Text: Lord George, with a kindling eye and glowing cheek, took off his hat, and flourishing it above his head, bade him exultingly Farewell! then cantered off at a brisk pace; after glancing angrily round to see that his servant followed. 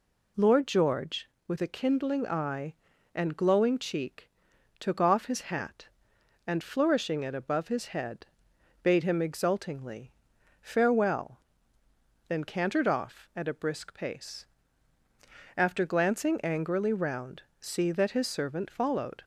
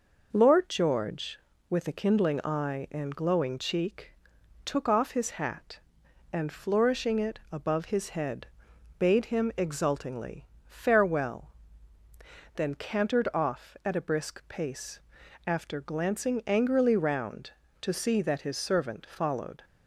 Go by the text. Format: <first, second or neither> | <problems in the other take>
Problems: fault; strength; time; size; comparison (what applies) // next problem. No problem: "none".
second | pauses between "exultingly" and "Farewell"; noticeable; at 10.1 s; 0.50 s long; slight in the second // skips "to"; at 17.5 s